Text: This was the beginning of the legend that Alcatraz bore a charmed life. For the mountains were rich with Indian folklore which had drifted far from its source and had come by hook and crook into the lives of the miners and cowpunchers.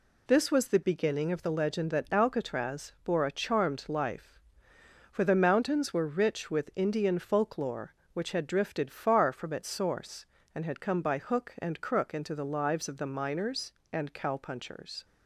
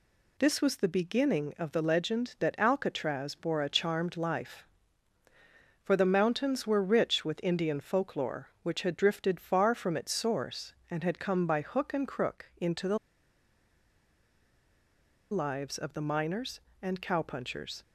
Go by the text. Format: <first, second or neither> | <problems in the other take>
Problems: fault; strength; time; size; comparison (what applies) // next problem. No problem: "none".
first | pauses between "the" and "lives"; strong; at 12.9 s; 2.3 s long